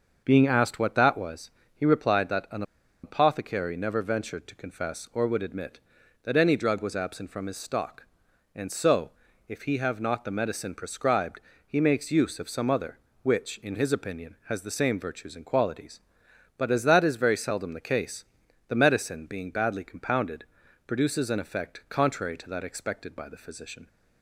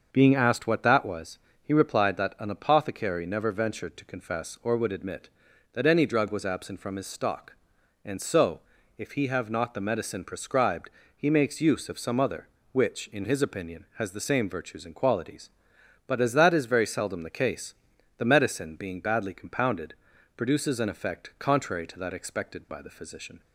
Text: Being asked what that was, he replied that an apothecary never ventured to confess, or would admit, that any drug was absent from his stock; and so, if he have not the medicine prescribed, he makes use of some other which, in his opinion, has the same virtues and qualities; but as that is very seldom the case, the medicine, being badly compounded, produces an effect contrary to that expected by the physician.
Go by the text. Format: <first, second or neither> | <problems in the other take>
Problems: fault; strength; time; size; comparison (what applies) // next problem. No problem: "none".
second | starts louder than the rest; until 1.2 s; 6.5 dB; also in the second // pauses between "an" and "apothecary"; at 2.6 s; 0.40 s long